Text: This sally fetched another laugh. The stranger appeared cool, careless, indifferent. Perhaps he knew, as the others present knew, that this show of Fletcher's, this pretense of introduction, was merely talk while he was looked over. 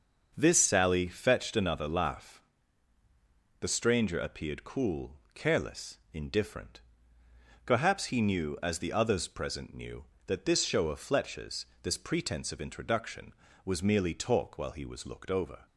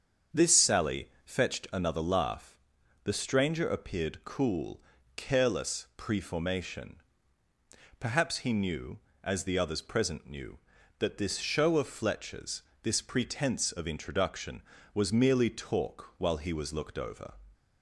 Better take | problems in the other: first | starts louder than the rest; until 1.5 s; 7 dB; also in the first // pauses between "sally" and "fetched"; slight; at 1.0 s; 0.16 s long // says "preformation" for "indifferent"; at 5.9 s

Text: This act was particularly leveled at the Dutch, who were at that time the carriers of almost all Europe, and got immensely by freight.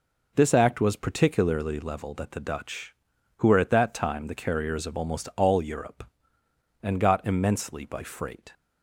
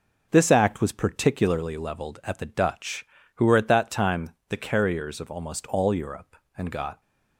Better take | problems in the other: first | pauses between "time" and "the"; slight; at 4.3 s; 0.18 s long // stops before "immensely by freight"; at 7.0 s

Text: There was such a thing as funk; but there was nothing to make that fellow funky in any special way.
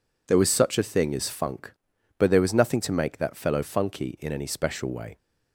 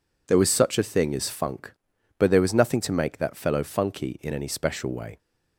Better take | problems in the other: neither | none

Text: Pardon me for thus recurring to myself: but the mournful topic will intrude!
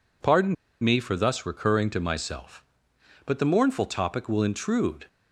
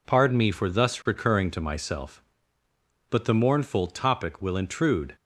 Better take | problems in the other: second | pauses between "Pardon" and "me"; slight; at 0.5 s; 0.26 s long

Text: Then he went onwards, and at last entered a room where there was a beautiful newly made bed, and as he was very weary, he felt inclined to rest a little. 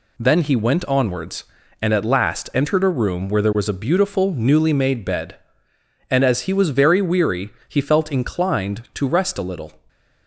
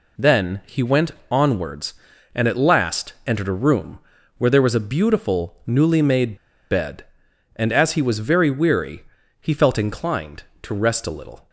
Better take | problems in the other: first | pauses between "went" and "onwards"; slight; at 1.1 s; 0.18 s long // pauses between "room" and "where"; at 3.9 s; 0.38 s long // pauses between "made" and "bed"; slight; at 6.3 s; 0.35 s long

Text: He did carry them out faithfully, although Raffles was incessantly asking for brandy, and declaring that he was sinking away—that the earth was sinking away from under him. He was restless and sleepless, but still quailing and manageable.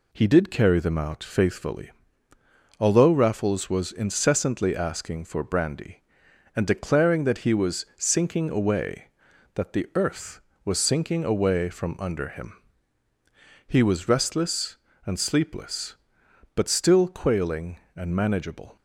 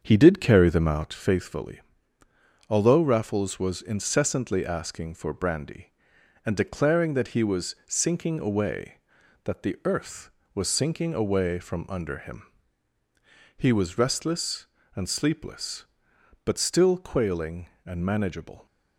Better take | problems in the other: first | starts louder than the rest; until 1.3 s; 7 dB

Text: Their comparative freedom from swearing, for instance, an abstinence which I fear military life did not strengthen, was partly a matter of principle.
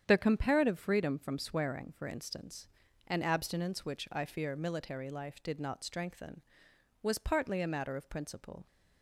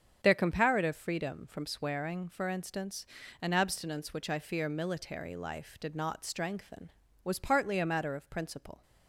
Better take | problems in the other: neither | starts louder than the rest; strong; the same in both

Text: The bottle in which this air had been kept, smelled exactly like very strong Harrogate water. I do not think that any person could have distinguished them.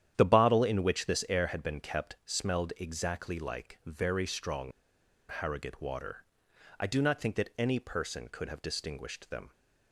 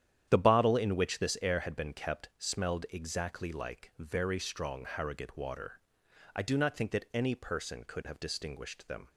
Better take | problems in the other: second | starts louder than the rest; strong; until 1.1 s; 10 dB; strong in the second // pauses between "strong" and "Harrogate"; noticeable; at 4.7 s; 0.57 s long

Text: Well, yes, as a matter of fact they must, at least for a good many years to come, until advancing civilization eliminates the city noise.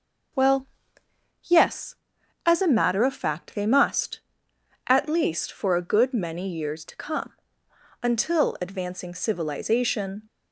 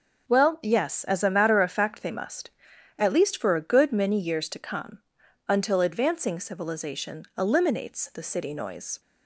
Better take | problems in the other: second | starts louder than the rest; noticeable; until 2.6 s; 6 dB; noticeable in the second // stops before "eliminates the city noise"; at 10.2 s

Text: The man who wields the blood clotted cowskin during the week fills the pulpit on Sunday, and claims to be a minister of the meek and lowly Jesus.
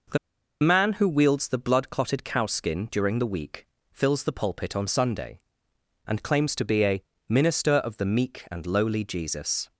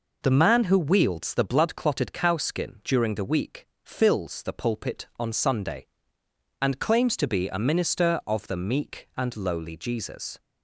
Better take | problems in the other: second | pauses between "The" and "man"; at 0.1 s; 0.43 s long // pauses between "week" and "fills"; slight; at 3.6 s; 0.24 s long; slight in the second // pauses between "a" and "minister"; slight; at 7.0 s; 0.28 s long

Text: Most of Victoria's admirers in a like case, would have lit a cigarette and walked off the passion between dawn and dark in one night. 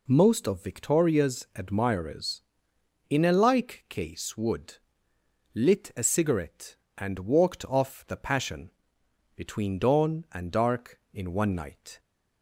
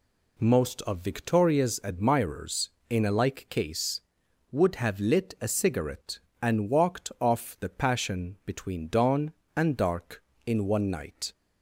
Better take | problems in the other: second | skips "have"; at 5.1 s // pauses between "passion" and "between"; noticeable; at 8.7 s; 0.64 s long

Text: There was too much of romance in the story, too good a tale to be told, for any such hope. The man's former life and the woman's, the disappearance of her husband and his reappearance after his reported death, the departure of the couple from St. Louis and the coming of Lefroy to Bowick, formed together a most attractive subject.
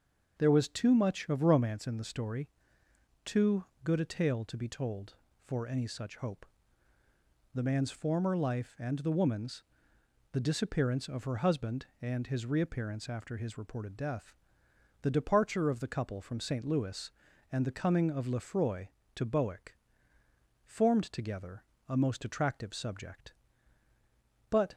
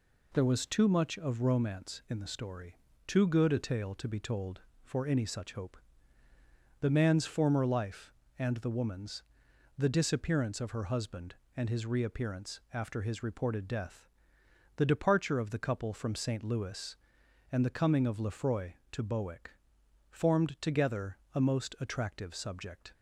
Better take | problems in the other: second | starts louder than the rest; until 1.4 s; 6 dB // pauses between "too" and "good"; slight; at 3.6 s; 0.20 s long // pauses between "together" and "a"; slight; at 21.6 s; 0.26 s long; slight in the second // goes on to say "But"; slight; from 24.4 s on; 0.24 s long

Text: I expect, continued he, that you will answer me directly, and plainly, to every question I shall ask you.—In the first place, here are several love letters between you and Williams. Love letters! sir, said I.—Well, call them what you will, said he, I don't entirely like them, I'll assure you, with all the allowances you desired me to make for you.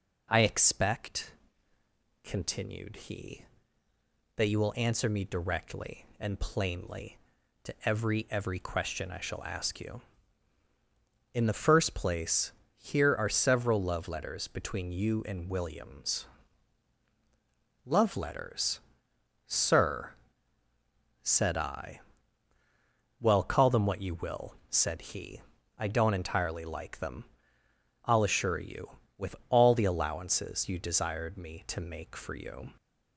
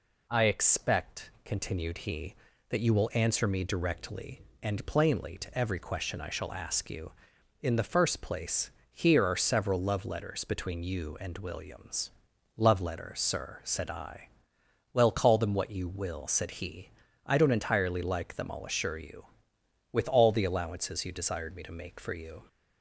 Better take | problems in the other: second | says "every" twice; at 8.2 s

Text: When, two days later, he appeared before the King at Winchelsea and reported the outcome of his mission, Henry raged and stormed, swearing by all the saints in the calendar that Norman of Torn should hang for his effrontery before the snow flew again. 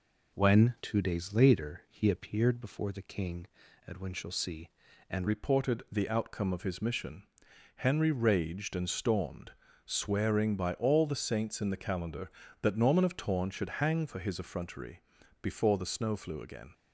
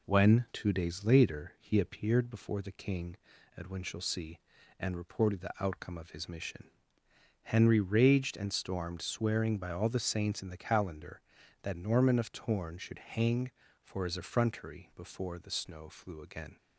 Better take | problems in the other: second | changes voice at "reported"; from 5.2 s on; 11.5 s long // pauses between "effrontery" and "before"; at 15.0 s; 0.40 s long

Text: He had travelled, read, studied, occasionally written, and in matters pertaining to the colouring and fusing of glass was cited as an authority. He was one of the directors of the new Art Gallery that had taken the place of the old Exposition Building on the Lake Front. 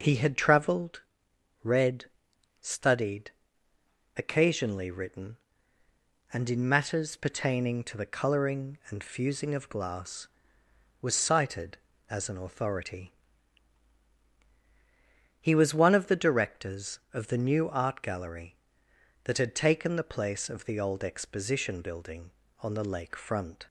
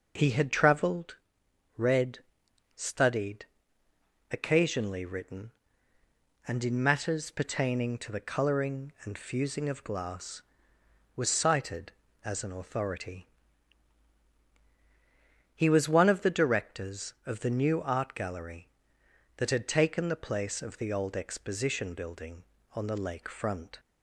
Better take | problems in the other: neither | none

